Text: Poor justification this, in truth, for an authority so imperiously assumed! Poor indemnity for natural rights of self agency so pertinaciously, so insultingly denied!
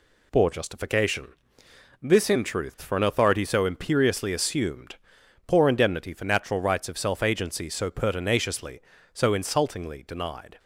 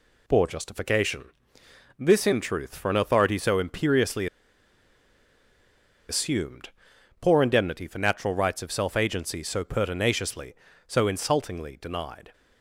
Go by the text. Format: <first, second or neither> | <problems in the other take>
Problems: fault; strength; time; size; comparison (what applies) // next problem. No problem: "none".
first | pauses between "justification" and "this"; noticeable; at 1.2 s; 0.72 s long; noticeable in the first // pauses between "imperiously" and "assumed"; strong; at 4.2 s; 1.8 s long